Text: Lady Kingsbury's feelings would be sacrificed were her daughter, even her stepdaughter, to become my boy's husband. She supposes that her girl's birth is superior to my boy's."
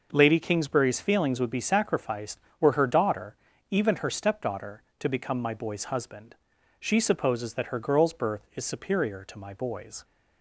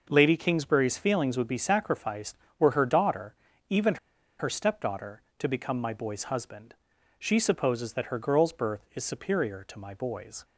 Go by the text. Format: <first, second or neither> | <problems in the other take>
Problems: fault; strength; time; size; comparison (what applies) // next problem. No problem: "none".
first | pauses between "even" and "her"; at 3.9 s; 0.43 s long